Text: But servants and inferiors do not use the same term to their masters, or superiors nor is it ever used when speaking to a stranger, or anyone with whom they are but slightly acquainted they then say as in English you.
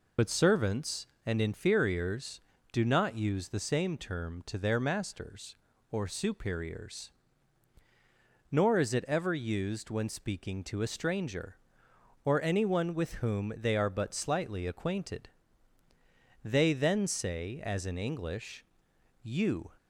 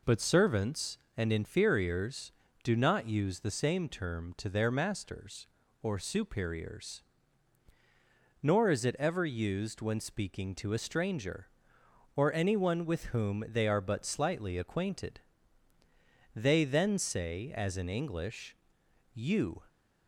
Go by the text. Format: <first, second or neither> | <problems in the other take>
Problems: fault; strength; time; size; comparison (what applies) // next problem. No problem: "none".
second | loses the start of "But"; at 0.1 s; 70 ms // pauses between "superiors" and "nor"; strong; at 7.1 s; 1.4 s long; strong in the second // pauses between "acquainted" and "they"; at 15.2 s; 1.1 s long; also in the second // pauses between "English" and "you"; noticeable; at 18.6 s; 0.60 s long; noticeable in the second